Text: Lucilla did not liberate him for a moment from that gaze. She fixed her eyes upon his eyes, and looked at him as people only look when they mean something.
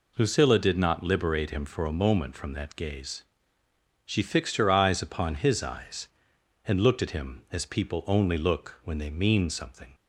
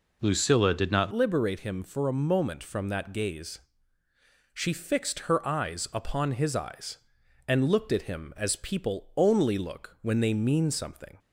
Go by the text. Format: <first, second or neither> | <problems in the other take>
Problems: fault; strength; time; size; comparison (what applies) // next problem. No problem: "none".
first | changes voice at "liberate"; from 1.1 s on; 10.0 s long